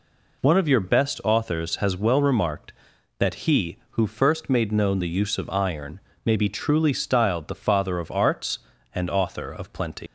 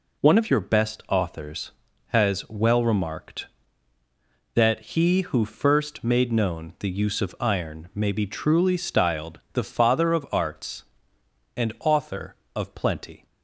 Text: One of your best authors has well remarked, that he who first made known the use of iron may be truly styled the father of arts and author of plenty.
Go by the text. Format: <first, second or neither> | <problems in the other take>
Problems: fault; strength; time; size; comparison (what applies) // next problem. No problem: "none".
second | pauses between "iron" and "may"; slight; at 5.9 s; 0.28 s long // leaves "plenty" unfinished; at 10.0 s; 110 ms